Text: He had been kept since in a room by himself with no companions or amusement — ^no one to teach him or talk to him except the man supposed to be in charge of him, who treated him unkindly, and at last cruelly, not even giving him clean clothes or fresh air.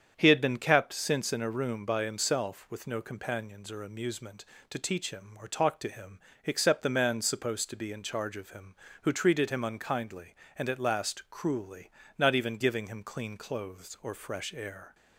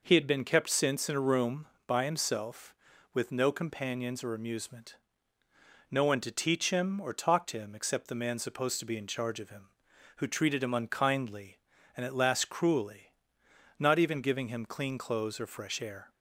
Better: second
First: starts louder than the rest; strong; until 1.1 s; 8 dB // skips "no one"; at 4.5 s // pauses between "him" and "except"; slight; at 6.2 s; 0.24 s long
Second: none

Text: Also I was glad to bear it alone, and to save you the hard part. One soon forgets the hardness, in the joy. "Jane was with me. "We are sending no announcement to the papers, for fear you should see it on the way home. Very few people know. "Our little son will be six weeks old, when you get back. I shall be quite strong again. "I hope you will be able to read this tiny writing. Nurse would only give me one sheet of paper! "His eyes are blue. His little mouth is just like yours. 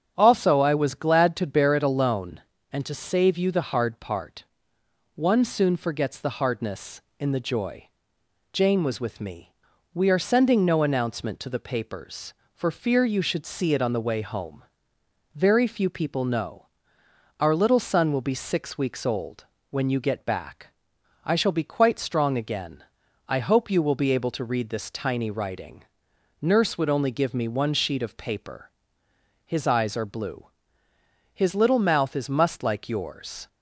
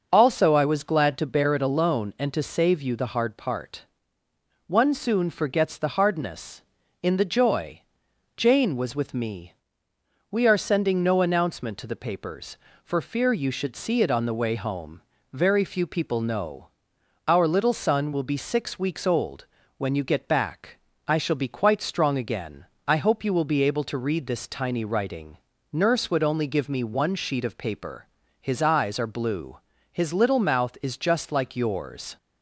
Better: second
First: starts louder than the rest; strong; until 1.1 s; 8 dB // says "must" for "just"; at 32.2 s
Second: none

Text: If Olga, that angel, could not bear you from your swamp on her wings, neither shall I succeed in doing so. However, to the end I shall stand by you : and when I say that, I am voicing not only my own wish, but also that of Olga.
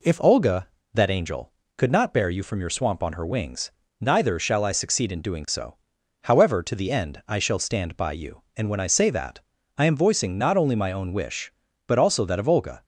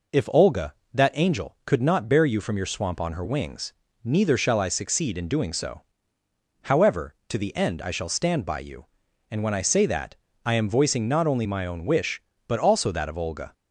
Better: neither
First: none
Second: none

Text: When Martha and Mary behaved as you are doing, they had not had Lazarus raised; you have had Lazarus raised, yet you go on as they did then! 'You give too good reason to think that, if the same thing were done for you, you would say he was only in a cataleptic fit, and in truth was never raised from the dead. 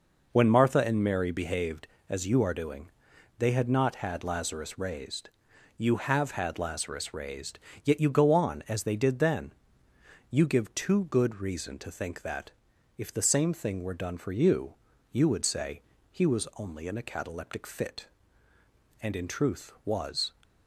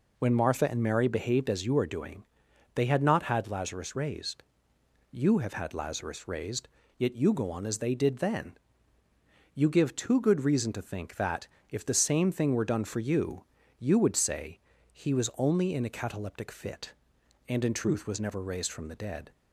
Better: second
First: pauses between "say" and "he"; slight; at 15.8 s; 0.30 s long // stops before "never raised from the dead"; at 20.4 s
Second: pauses between "say" and "he"; slight; at 14.5 s; 0.34 s long

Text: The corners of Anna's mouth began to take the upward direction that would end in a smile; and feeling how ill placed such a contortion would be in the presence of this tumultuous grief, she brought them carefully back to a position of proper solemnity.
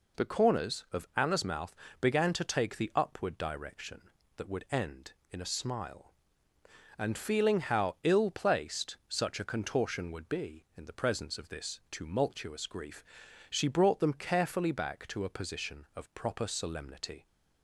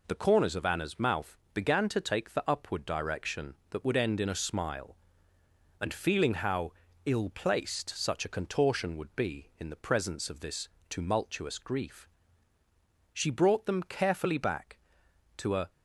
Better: first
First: pauses between "mouth" and "began"; slight; at 1.7 s; 0.26 s long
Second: pauses between "mouth" and "began"; slight; at 1.3 s; 0.18 s long // pauses between "how" and "ill"; slight; at 6.7 s; 0.34 s long // pauses between "this" and "tumultuous"; slight; at 10.6 s; 0.20 s long // stops before "position of proper solemnity"; at 15.6 s

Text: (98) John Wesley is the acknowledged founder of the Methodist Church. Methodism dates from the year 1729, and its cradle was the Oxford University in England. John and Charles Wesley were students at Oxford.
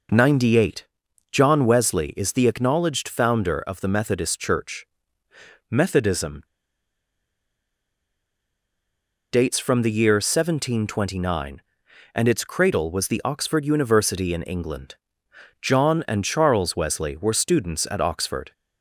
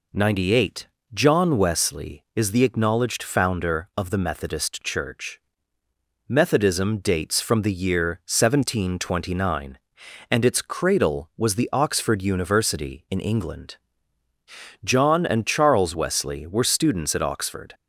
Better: second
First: pauses between "Methodism" and "dates"; strong; at 6.4 s; 2.8 s long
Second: none

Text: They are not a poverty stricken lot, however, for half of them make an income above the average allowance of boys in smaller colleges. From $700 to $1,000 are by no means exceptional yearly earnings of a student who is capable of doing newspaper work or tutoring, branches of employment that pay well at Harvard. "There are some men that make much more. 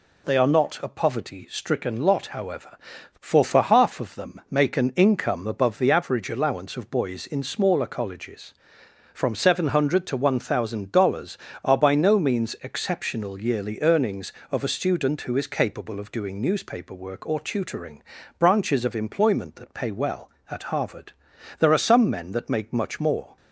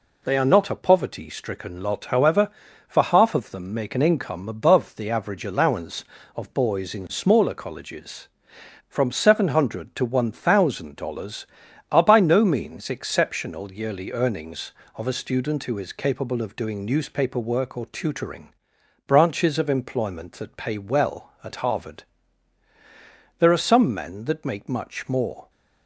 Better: second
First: says "for" twice; at 3.4 s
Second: none

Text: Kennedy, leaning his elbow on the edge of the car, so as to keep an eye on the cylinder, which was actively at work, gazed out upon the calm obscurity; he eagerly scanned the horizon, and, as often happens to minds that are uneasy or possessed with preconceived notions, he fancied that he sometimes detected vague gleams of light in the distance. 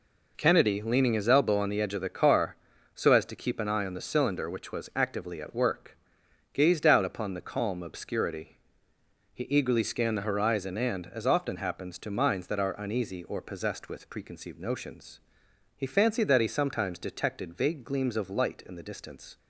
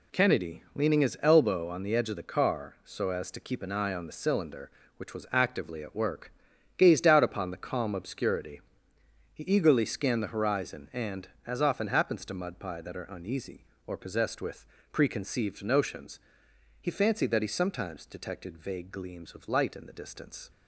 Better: first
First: none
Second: says "mudpie" for "minds"; at 12.3 s // pauses between "with" and "preconceived"; slight; at 14.6 s; 0.28 s long

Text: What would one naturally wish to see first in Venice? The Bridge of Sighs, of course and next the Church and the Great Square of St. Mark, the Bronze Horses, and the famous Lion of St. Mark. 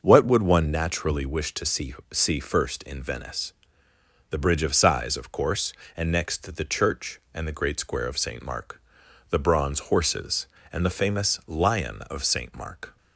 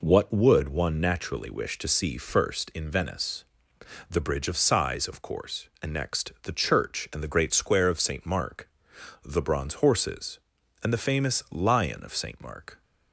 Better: second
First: starts louder than the rest; noticeable; until 1.0 s; 6 dB // says "see" twice; at 2.1 s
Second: none

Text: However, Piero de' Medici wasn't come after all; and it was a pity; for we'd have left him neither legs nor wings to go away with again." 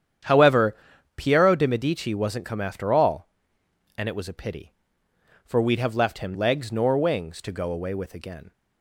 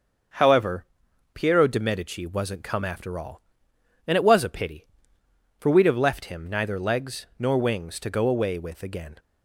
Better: second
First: starts louder than the rest; strong; until 1.6 s; 9 dB // skips "neither"; at 6.3 s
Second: starts louder than the rest; until 1.7 s; 6.5 dB

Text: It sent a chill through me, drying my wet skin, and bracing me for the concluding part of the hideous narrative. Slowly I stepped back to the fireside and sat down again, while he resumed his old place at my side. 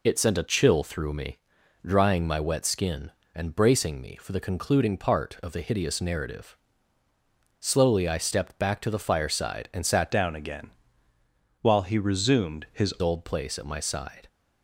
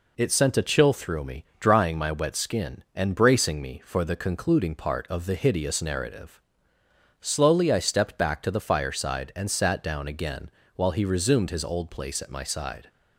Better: second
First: changes voice from "down" to "his"; from 10.1 to 12.9 s; 2.8 s long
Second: none

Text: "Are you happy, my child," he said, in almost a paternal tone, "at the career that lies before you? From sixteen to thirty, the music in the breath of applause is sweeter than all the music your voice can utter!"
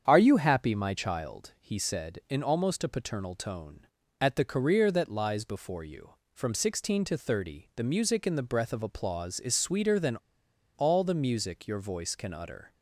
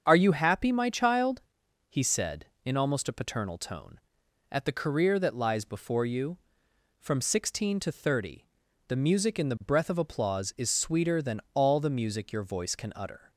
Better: second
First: starts louder than the rest; strong; until 1.0 s; 7.5 dB // pauses between "than" and "all"; noticeable; at 10.1 s; 0.60 s long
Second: starts louder than the rest; strong; until 1.0 s; 7 dB

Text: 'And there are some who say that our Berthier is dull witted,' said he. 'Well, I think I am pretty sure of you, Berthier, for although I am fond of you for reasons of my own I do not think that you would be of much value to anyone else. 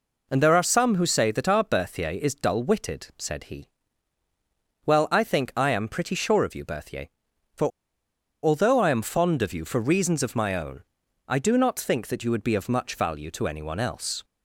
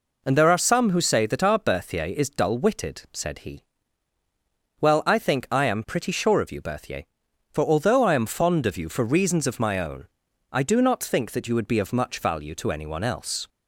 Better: second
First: pauses between "for" and "although"; noticeable; at 7.6 s; 0.75 s long // pauses between "own" and "I"; noticeable; at 10.8 s; 0.48 s long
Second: pauses between "own" and "I"; noticeable; at 10.0 s; 0.48 s long

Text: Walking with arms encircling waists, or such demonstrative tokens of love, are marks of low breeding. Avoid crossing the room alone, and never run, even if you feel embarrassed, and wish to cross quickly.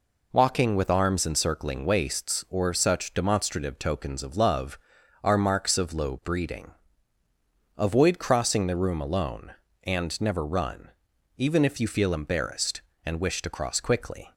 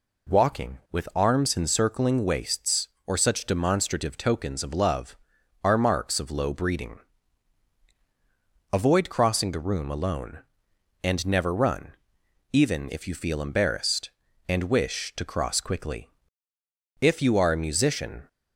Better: first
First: none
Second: goes on to say "If you are a musician"; noticeable; from 17.0 s on; 1.2 s long

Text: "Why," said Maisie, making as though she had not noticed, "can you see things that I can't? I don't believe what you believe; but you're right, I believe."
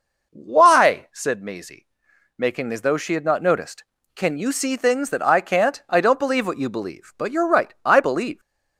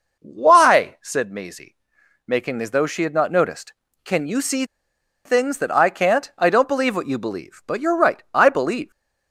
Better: first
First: none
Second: pauses between "see" and "things"; noticeable; at 4.6 s; 0.61 s long

